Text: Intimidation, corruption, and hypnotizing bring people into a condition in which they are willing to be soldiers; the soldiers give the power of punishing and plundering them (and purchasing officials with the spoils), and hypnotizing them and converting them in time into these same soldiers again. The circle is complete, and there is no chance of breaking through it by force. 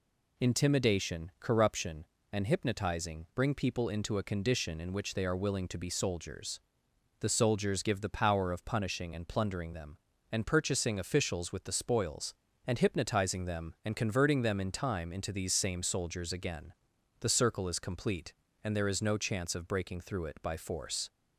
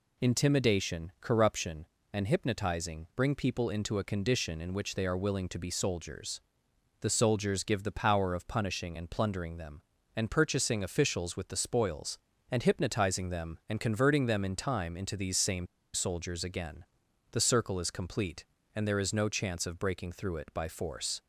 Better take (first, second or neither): first